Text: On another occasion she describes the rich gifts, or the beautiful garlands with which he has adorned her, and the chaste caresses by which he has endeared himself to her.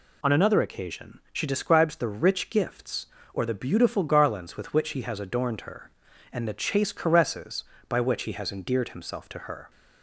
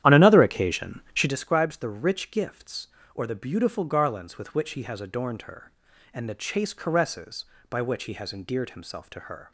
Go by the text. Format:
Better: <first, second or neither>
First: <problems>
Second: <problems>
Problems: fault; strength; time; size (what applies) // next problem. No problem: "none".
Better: first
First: none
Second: starts louder than the rest; strong; until 1.3 s; 11 dB